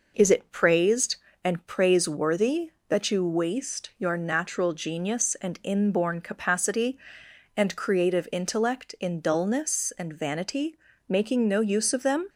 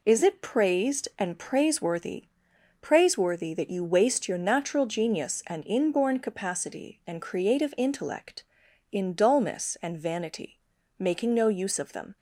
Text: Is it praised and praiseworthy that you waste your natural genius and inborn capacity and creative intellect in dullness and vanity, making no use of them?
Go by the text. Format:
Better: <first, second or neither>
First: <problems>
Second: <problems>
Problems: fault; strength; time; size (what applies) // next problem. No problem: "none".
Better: first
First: none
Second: says "praiseworthy" twice; at 2.8 s